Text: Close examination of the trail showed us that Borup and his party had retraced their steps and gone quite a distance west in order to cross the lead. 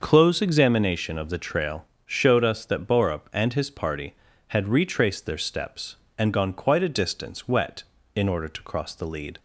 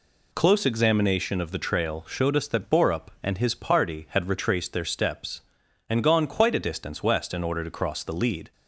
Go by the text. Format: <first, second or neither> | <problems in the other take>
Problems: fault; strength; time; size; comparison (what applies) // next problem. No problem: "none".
second | starts louder than the rest; until 1.0 s; 6 dB // pauses between "trail" and "showed"; slight; at 1.8 s; 0.20 s long // says "wet" for "west"; at 7.4 s